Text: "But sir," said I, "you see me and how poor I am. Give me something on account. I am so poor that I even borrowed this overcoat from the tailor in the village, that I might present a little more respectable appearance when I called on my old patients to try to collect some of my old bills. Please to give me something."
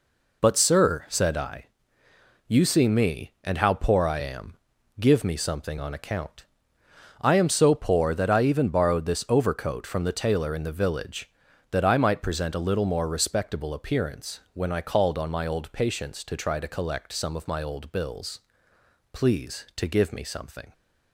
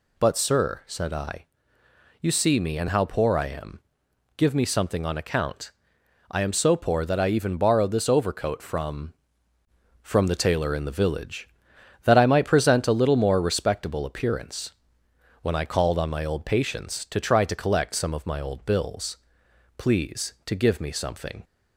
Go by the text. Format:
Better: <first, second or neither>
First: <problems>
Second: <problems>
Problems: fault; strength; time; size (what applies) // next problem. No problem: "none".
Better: first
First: none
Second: says "from" twice; at 10.0 s // pauses between "appearance" and "when"; noticeable; at 14.7 s; 0.68 s long